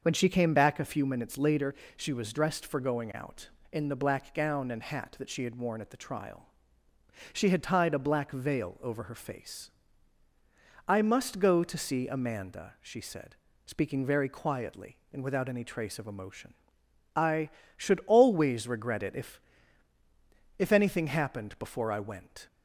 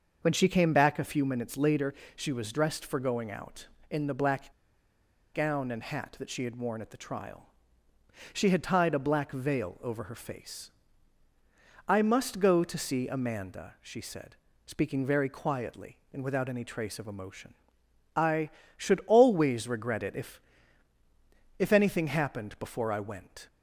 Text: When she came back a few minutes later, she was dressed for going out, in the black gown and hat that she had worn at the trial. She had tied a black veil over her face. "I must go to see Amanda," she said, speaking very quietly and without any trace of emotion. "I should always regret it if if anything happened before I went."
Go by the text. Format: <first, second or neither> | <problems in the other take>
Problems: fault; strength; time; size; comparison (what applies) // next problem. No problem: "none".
first | starts louder than the rest; until 1.2 s; 6.5 dB; also in the first // pauses between "black" and "gown"; noticeable; at 4.5 s; 0.82 s long // pauses between "if" and "if"; at 20.4 s; 1.1 s long; also in the first